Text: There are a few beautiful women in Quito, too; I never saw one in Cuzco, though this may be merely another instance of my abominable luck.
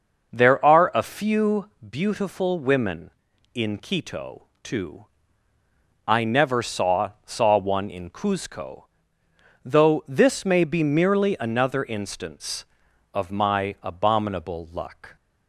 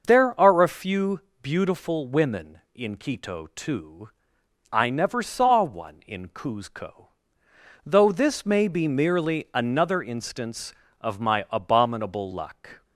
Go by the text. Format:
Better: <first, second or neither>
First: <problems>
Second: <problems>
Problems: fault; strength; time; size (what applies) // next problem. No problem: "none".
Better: second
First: pauses between "few" and "beautiful"; slight; at 1.6 s; 0.20 s long // says "saw" twice; at 7.2 s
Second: pauses between "few" and "beautiful"; slight; at 1.2 s; 0.20 s long